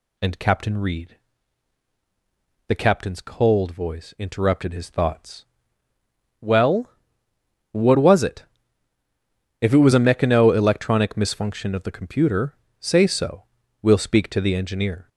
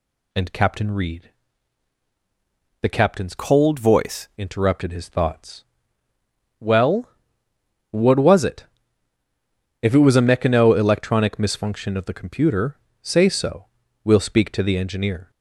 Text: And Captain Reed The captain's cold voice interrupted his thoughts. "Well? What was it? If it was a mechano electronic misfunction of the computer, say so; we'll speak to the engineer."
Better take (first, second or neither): first